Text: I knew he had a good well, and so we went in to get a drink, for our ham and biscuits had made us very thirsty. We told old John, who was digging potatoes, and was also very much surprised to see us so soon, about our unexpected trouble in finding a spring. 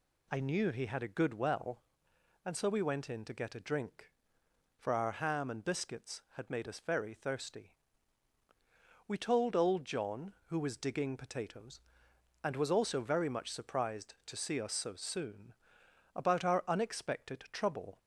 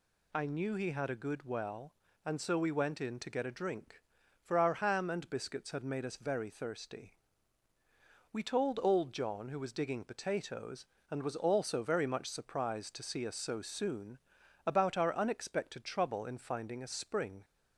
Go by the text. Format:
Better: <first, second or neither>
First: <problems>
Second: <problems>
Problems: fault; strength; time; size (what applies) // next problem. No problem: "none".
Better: second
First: stops before "in finding a spring"; at 17.9 s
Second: none